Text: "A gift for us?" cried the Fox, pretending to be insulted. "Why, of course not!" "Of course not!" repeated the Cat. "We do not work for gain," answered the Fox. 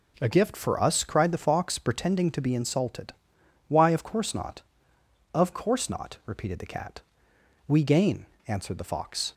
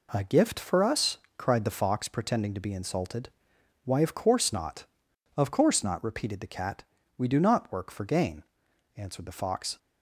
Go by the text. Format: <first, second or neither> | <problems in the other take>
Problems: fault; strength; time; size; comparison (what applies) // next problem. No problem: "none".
second | skips "do not work for"; at 7.8 s